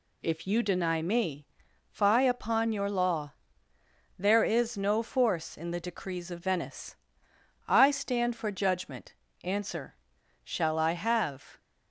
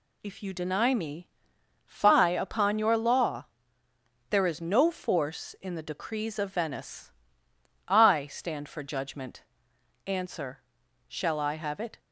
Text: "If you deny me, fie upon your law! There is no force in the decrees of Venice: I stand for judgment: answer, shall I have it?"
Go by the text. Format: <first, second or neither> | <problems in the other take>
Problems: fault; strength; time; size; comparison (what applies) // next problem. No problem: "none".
second | stops before "it"; at 11.5 s